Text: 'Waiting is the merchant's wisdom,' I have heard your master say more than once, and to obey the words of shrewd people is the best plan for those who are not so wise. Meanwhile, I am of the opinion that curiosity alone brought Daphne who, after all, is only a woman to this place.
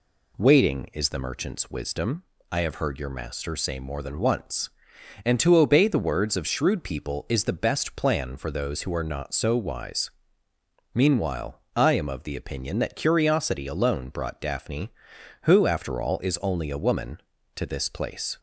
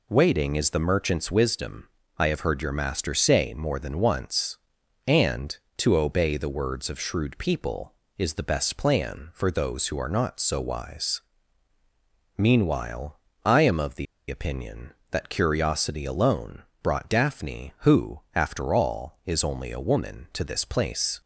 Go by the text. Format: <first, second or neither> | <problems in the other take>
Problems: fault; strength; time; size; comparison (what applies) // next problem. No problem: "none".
first | pauses between "the" and "opinion"; slight; at 14.0 s; 0.22 s long // pauses between "alone" and "brought"; slight; at 16.6 s; 0.18 s long